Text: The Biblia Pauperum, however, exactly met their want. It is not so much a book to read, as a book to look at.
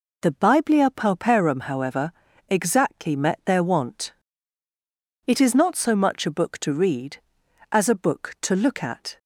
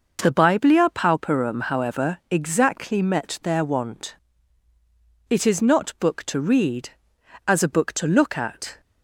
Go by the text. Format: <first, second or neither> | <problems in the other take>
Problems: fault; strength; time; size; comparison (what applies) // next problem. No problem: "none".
first | skips "so much a"; at 5.9 s